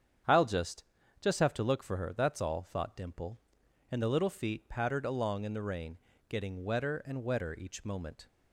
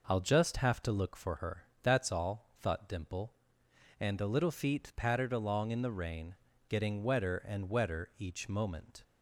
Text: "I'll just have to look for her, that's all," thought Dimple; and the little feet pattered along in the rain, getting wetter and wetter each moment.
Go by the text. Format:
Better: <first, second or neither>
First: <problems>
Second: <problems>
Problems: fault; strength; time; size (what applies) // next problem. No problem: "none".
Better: second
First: starts louder than the rest; strong; until 1.6 s; 8 dB // says "just" twice; at 1.1 s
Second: none